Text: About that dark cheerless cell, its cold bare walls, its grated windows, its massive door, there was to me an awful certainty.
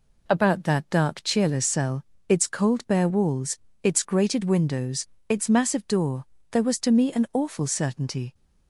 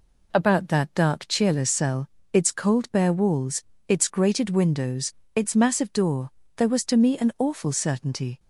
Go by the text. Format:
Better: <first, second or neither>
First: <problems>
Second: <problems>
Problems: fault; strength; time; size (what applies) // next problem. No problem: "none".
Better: neither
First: none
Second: none